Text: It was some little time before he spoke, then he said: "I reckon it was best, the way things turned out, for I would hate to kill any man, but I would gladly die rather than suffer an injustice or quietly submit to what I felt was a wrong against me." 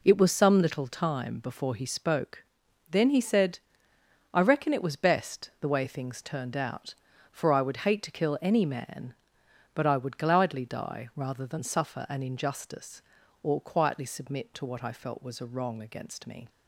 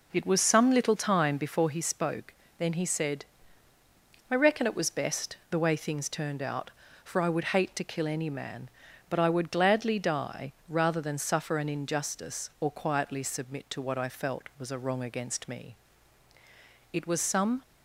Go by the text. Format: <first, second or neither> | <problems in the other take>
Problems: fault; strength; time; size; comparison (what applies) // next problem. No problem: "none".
first | pauses between "die" and "rather"; slight; at 10.5 s; 0.16 s long // goes on to say "It was some"; noticeable; from 16.9 s on; 0.70 s long